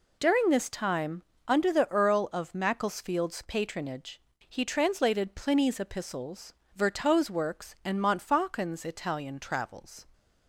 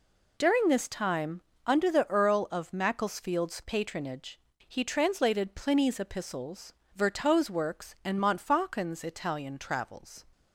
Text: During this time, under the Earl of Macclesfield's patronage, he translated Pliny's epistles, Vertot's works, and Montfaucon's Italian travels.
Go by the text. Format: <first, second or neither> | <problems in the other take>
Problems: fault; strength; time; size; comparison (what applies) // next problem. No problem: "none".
neither | none